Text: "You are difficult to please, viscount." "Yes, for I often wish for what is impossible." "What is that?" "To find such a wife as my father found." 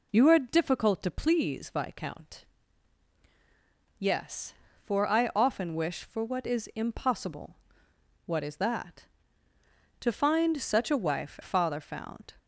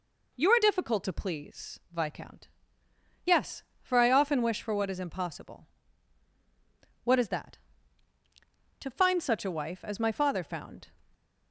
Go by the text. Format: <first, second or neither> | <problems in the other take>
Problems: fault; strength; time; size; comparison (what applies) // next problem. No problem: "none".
second | skips "as my"; at 11.4 s